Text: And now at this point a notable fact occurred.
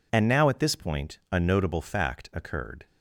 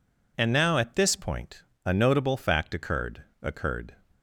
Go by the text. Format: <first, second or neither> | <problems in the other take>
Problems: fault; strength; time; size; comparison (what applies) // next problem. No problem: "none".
first | pauses between "point" and "a"; slight; at 1.6 s; 0.22 s long // says "occurred" twice; at 3.4 s